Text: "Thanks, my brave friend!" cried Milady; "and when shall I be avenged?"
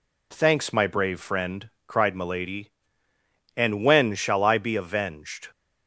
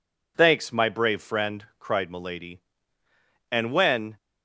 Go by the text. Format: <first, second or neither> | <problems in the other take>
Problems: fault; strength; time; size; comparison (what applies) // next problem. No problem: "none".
first | stops before "shall I be avenged"; at 4.1 s